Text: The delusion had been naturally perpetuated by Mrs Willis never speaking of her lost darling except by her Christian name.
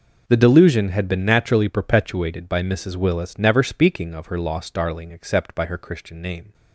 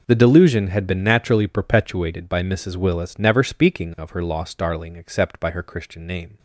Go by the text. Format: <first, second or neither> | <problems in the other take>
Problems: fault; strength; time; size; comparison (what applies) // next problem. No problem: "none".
neither | none